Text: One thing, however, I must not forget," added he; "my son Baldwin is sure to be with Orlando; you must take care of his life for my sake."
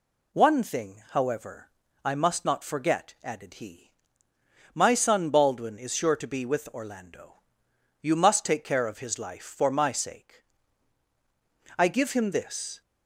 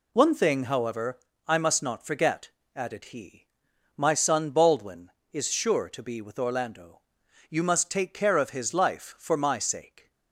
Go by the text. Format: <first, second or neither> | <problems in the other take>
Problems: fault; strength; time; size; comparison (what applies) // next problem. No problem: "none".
second | goes on to say "I give him this"; noticeable; from 11.7 s on; 1.0 s long